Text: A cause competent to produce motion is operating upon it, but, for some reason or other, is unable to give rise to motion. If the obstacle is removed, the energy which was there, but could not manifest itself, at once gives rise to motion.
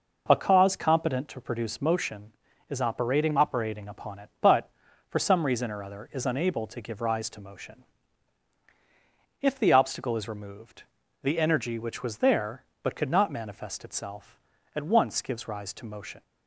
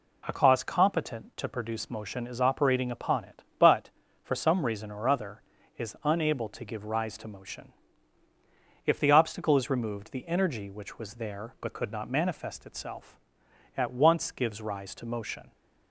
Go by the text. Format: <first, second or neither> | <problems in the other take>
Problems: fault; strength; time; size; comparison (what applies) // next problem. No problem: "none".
second | says "operating" twice; at 3.3 s